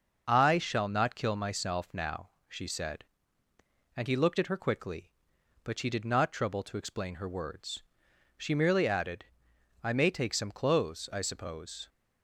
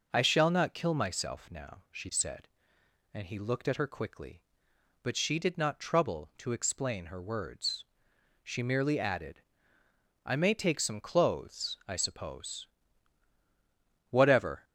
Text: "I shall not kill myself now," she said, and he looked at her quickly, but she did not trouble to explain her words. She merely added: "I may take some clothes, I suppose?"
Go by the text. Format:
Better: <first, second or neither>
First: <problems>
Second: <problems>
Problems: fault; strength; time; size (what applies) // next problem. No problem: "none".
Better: first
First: none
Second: goes on to say "Whatever"; from 14.0 s on; 0.54 s long